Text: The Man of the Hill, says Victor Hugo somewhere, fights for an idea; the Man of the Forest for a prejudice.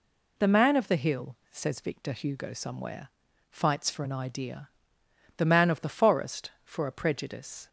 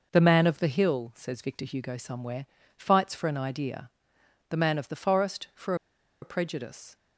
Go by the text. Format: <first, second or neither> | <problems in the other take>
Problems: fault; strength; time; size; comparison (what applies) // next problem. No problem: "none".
first | pauses between "for" and "a"; noticeable; at 5.7 s; 0.47 s long